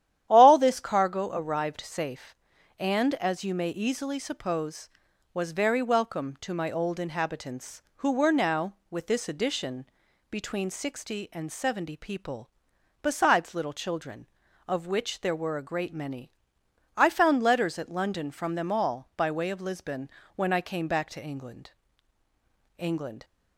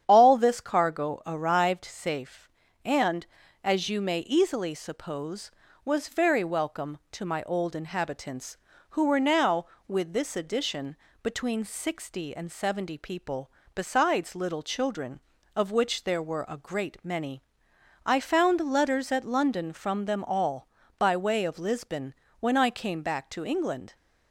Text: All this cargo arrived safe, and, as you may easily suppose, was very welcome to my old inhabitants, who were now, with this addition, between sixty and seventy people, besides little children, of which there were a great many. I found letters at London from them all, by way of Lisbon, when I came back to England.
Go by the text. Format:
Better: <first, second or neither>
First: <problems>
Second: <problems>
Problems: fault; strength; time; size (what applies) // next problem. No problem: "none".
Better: second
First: starts louder than the rest; strong; until 1.3 s; 11 dB // says "England" twice; at 22.7 s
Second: starts louder than the rest; strong; until 1.0 s; 9 dB